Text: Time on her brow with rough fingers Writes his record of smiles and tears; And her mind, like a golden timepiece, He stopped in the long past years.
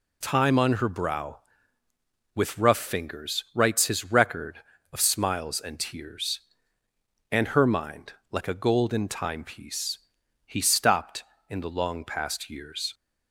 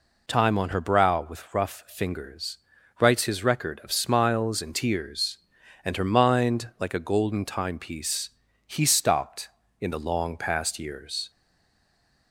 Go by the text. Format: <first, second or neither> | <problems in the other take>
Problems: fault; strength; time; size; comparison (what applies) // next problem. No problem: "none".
first | pauses between "fingers" and "Writes"; at 2.5 s; 0.42 s long // stays silent after the last word; from 11.3 s on; 1.0 s long